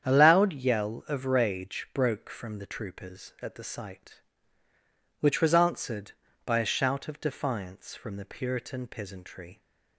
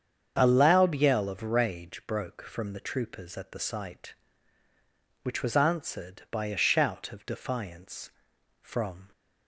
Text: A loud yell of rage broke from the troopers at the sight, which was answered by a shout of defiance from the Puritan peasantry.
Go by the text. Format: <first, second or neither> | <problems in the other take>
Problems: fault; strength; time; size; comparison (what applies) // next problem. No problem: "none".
first | starts louder than the rest; strong; until 1.3 s; 7.5 dB; strong in the first // stops before "the Puritan peasantry"; at 9.1 s